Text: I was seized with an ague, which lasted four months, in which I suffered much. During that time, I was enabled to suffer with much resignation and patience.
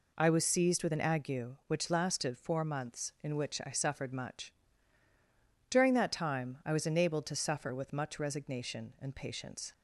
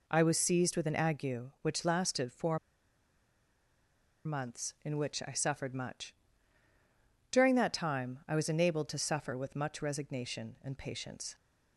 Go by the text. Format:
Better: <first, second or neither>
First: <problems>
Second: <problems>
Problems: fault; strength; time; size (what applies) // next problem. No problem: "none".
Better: first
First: none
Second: pauses between "four" and "months"; strong; at 2.5 s; 1.6 s long